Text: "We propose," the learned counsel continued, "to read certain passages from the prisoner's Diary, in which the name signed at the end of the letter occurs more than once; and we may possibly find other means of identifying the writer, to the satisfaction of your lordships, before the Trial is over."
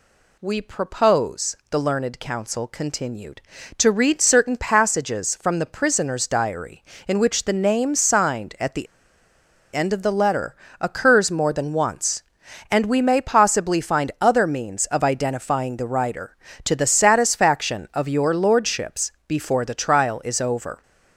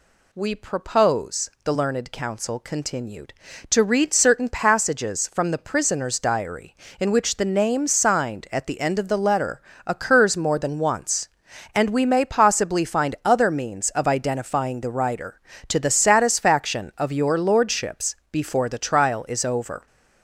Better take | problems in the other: second | pauses between "the" and "end"; noticeable; at 8.8 s; 0.87 s long // pauses between "letter" and "occurs"; slight; at 10.5 s; 0.28 s long; slight in the second

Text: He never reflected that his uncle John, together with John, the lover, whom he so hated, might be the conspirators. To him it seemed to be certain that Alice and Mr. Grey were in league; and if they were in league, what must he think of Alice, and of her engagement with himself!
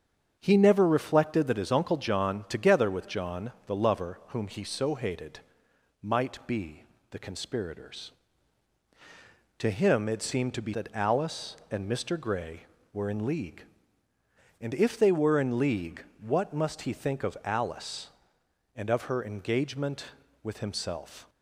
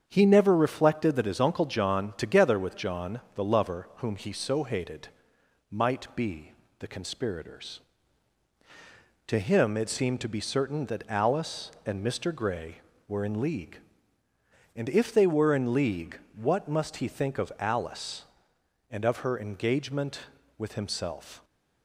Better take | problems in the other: second | starts louder than the rest; strong; until 1.4 s; 7.5 dB; strong in the second // pauses between "be" and "the"; slight; at 6.8 s; 0.26 s long; slight in the second // skips "certain"; at 10.7 s

